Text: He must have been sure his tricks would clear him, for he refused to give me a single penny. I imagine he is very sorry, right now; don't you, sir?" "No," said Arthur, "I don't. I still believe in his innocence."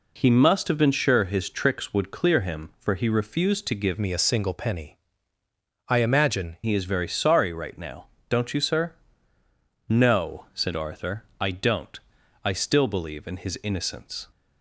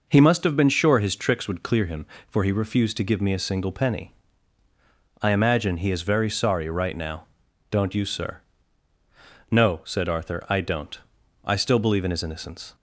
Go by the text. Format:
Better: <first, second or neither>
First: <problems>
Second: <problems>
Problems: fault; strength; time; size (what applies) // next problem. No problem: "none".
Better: second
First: changes voice from "me" to "imagine"; from 3.9 to 6.5 s; 2.6 s long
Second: none